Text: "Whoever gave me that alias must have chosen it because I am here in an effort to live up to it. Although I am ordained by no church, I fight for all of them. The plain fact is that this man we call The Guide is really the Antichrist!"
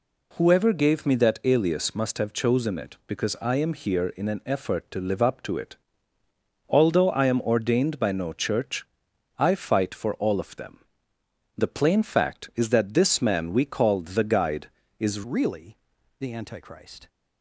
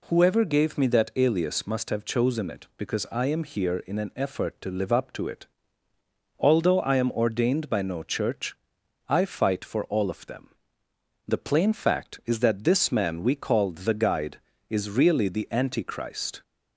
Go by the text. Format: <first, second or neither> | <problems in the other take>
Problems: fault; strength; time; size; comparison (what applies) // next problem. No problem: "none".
second | changes voice at "really"; from 15.2 s on; 1.8 s long // pauses between "really" and "the"; at 15.7 s; 0.42 s long